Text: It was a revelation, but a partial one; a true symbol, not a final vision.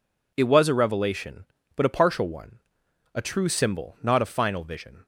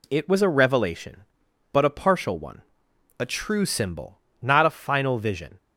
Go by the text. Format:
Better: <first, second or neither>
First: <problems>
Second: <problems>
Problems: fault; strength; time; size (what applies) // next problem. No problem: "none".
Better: neither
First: none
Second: none